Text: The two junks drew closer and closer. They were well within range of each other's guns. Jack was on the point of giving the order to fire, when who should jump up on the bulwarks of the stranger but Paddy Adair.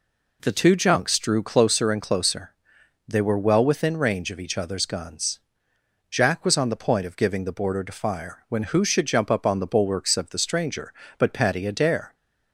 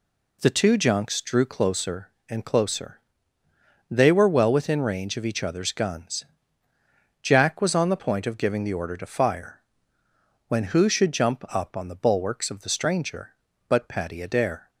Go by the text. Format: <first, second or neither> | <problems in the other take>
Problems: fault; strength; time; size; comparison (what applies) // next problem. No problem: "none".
second | says "border" for "order"; at 7.5 s